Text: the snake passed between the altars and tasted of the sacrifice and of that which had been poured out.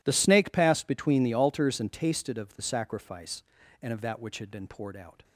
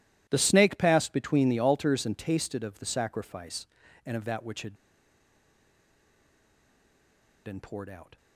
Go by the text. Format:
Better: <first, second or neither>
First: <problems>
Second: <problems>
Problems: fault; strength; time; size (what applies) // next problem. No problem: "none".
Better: first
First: none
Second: pauses between "had" and "been"; strong; at 4.7 s; 2.7 s long